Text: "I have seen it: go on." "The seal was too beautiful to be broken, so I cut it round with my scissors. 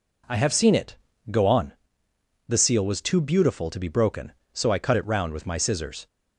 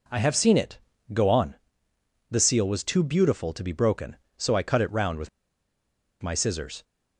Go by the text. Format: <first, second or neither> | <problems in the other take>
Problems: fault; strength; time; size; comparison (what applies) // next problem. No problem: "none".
first | pauses between "with" and "my"; noticeable; at 5.2 s; 0.93 s long